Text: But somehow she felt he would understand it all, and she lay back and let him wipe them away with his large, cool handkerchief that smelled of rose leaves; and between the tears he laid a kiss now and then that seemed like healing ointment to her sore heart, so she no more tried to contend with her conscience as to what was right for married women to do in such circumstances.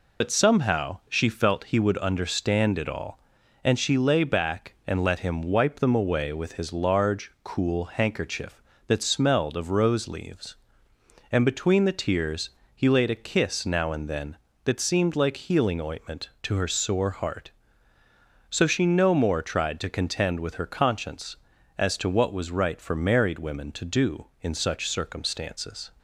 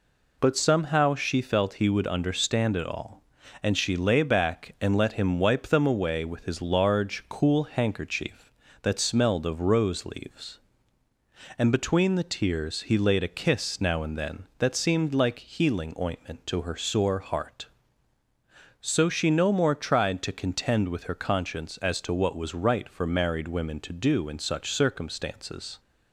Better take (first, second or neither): second